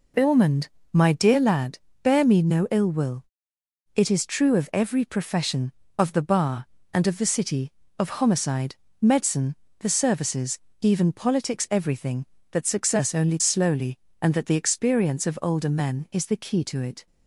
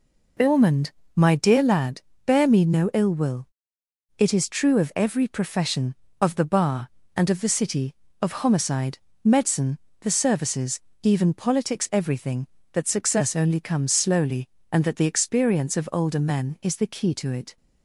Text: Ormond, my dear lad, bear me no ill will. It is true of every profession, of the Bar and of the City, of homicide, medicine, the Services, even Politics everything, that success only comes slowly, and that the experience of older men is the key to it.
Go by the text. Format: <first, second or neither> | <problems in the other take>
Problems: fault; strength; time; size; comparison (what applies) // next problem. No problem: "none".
second | skips "comes"; at 13.4 s